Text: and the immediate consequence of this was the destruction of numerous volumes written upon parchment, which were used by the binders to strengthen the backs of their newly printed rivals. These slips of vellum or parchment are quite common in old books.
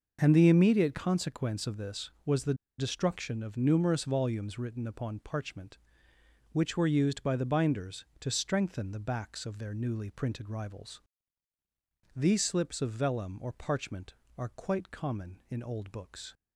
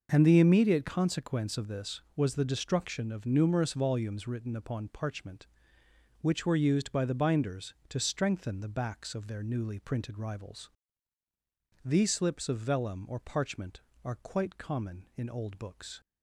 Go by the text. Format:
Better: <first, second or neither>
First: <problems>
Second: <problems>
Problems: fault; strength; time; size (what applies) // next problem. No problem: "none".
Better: second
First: pauses between "the" and "destruction"; slight; at 2.5 s; 0.24 s long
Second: none